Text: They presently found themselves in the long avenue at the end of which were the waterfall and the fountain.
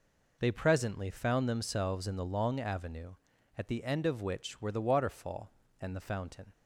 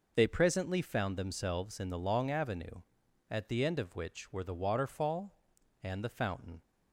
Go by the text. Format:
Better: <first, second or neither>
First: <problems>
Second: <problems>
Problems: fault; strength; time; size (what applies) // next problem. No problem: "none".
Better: neither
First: none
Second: none